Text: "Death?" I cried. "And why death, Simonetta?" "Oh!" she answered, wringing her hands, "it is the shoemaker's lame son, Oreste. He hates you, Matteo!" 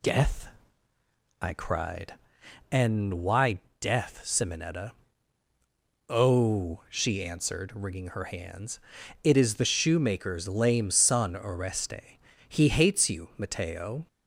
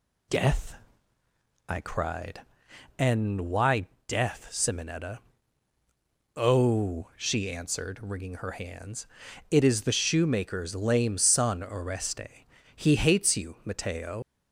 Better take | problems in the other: first | pauses between "why" and "death"; slight; at 3.8 s; 0.20 s long; slight in the first // leaves "Matteo" unfinished; at 14.2 s; 115 ms

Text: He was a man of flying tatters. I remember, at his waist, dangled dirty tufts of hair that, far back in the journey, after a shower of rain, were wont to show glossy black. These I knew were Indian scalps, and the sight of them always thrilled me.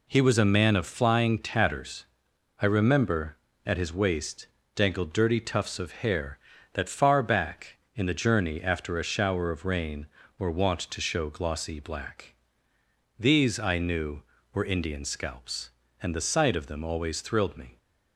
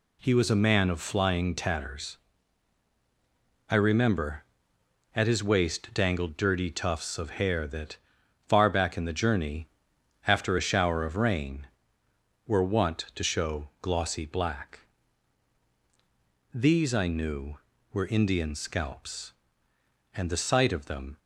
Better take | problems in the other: first | stops before "always thrilled me"; at 21.1 s

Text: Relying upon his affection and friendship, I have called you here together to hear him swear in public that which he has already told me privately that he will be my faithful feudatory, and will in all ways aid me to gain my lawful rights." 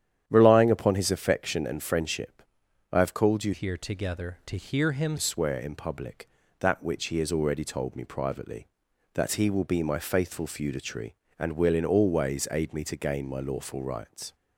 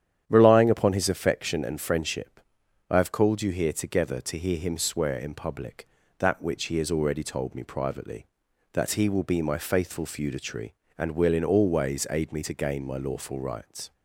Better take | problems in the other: second | starts louder than the rest; strong; until 1.2 s; 10 dB; strong in the second // changes voice from "here" to "him"; from 3.5 to 5.1 s; 1.6 s long

